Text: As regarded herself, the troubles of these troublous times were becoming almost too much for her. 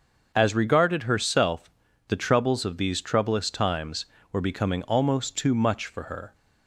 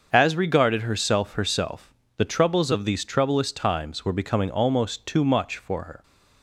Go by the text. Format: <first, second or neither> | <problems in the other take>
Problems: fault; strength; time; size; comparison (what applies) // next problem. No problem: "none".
first | starts louder than the rest; until 1.1 s; 6.5 dB; also in the first // says "herself" twice; at 1.3 s